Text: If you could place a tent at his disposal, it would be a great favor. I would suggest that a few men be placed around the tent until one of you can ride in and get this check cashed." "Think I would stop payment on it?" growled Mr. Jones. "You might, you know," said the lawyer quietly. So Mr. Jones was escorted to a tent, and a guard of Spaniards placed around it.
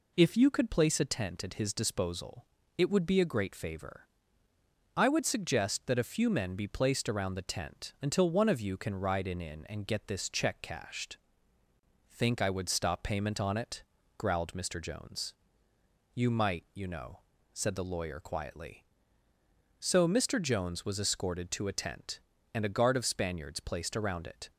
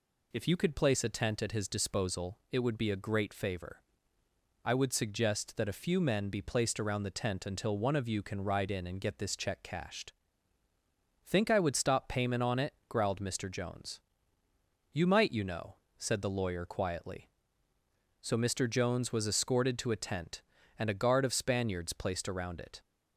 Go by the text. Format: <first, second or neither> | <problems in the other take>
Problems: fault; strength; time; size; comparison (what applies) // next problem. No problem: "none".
second | says "in" twice; at 9.4 s